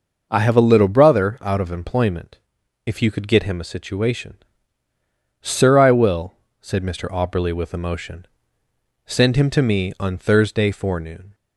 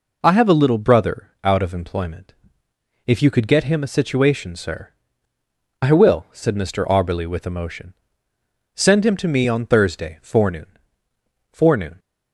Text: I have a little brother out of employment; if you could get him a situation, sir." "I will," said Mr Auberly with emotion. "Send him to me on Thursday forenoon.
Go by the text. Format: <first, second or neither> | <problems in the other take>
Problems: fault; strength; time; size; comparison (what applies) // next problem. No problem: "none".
first | says "forenoon" twice; at 11.5 s